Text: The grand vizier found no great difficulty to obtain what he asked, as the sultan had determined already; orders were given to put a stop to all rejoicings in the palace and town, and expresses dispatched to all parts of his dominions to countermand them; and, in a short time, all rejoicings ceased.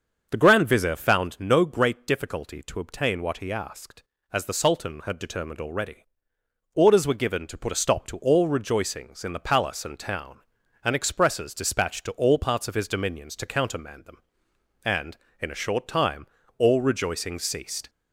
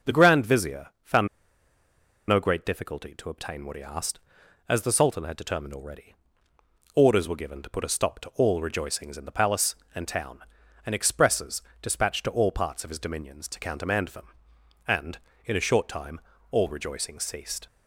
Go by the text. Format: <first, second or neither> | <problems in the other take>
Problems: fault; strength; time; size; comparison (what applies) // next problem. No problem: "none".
first | starts louder than the rest; noticeable; until 1.1 s; 6 dB; also in the first // pauses between "vizier" and "found"; slight; at 0.8 s; 0.16 s long // pauses between "found" and "no"; at 1.2 s; 1.0 s long // pauses between "expresses" and "dispatched"; slight; at 11.6 s; 0.20 s long